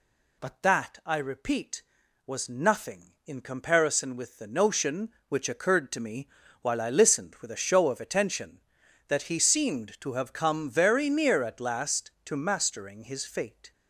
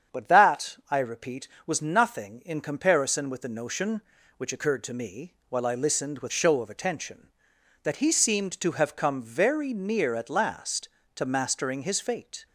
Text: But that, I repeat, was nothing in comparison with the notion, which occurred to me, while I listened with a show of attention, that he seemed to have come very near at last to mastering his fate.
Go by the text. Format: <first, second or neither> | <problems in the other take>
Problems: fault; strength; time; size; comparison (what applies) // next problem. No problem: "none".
first | starts louder than the rest; strong; until 1.2 s; 7.5 dB // skips "a"; at 6.3 s